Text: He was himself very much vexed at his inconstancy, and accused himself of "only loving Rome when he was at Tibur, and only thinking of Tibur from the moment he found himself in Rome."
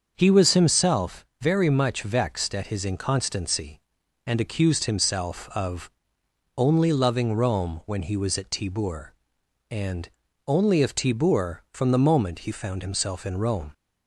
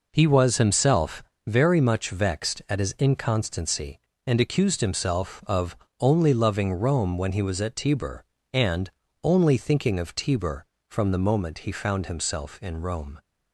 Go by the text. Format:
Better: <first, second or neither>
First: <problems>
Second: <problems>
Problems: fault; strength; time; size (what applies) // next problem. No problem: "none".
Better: second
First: starts louder than the rest; until 1.1 s; 6.5 dB // pauses between "himself" and "very"; slight; at 1.2 s; 0.16 s long // pauses between "of" and "only"; noticeable; at 5.9 s; 0.66 s long // pauses between "and" and "only"; at 10.0 s; 0.38 s long // skips "thinking"; at 10.8 s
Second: pauses between "himself" and "very"; slight; at 1.2 s; 0.22 s long // pauses between "of" and "only"; slight; at 5.7 s; 0.22 s long // pauses between "and" and "only"; slight; at 8.8 s; 0.34 s long